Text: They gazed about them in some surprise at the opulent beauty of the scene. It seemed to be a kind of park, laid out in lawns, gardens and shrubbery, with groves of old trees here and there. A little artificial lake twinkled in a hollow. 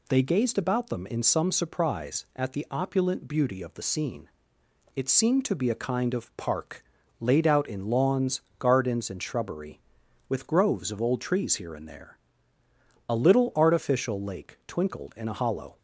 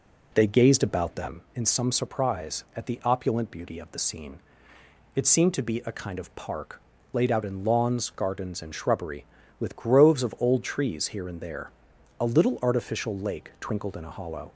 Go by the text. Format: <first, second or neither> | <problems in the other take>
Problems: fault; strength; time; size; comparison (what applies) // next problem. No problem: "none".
first | starts louder than the rest; slight; until 1.3 s; 2.5 dB